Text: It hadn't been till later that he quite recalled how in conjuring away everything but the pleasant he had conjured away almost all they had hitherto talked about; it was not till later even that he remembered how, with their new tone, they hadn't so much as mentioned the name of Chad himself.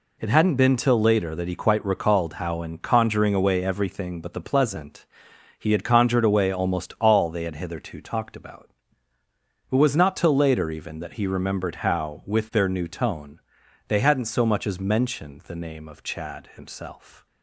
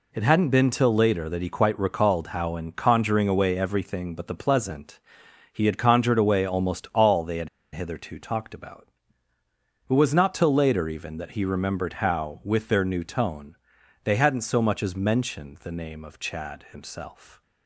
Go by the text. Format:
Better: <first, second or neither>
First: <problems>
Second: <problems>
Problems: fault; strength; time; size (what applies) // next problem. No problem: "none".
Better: first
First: pauses between "pleasant" and "he"; noticeable; at 5.0 s; 0.54 s long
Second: pauses between "pleasant" and "he"; noticeable; at 4.9 s; 0.54 s long // pauses between "had" and "hitherto"; slight; at 7.4 s; 0.25 s long